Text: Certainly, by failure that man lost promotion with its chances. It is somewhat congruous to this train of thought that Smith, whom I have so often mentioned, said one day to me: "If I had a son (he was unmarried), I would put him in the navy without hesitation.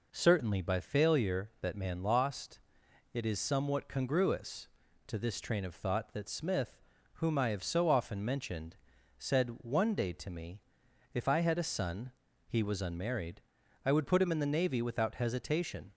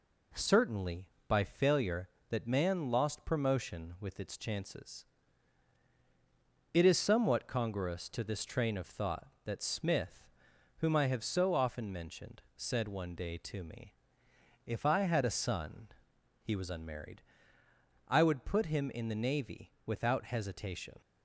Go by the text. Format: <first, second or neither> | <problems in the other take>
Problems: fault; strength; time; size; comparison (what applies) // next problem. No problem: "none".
second | skips "promotion with its chances"; at 2.8 s